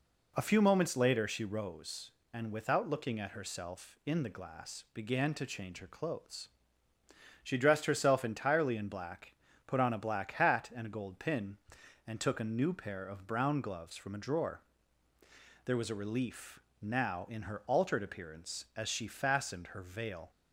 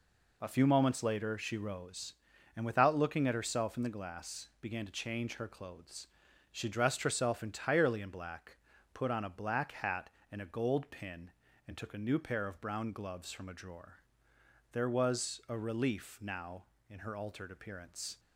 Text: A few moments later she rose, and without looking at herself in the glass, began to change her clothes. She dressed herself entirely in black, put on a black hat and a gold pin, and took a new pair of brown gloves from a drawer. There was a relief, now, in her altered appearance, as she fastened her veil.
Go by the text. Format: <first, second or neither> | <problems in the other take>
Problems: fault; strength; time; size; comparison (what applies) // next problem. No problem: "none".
first | stops before "as she fastened her veil"; at 18.1 s